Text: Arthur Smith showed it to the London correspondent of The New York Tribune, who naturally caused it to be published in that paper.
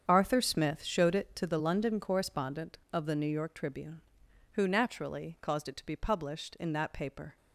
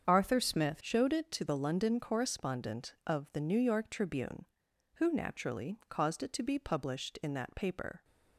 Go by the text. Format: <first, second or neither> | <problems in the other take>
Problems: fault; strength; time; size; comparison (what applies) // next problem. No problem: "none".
first | starts louder than the rest; strong; until 1.0 s; 7.5 dB; strong in the first // changes voice at "showed"; from 0.8 s on; 7.2 s long